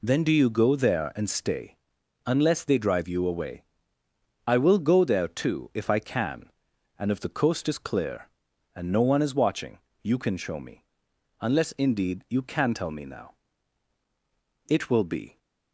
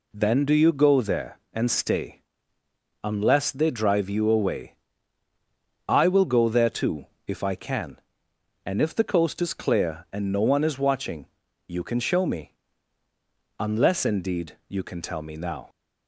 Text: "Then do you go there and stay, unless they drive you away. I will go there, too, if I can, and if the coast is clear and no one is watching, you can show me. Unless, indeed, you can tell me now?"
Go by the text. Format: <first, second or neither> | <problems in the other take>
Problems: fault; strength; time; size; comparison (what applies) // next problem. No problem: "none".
second | goes on to say "It will be"; noticeable; from 14.6 s on; 0.70 s long